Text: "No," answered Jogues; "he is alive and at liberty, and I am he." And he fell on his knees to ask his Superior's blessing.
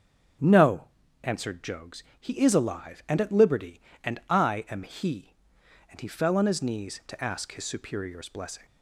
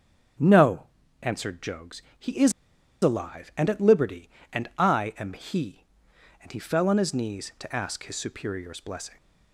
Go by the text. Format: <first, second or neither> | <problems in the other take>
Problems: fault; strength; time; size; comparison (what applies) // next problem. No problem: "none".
first | starts louder than the rest; until 1.7 s; 6.5 dB; also in the first // pauses between "is" and "alive"; noticeable; at 2.5 s; 0.50 s long